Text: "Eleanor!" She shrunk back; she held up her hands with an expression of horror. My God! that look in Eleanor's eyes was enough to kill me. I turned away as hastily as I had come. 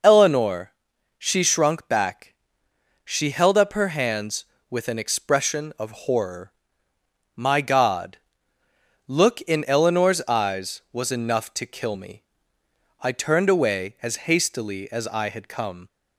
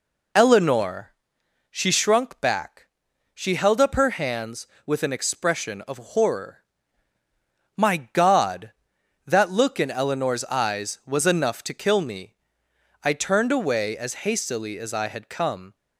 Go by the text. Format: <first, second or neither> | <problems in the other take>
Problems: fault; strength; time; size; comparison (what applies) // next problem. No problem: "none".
second | skips "that"; at 8.6 s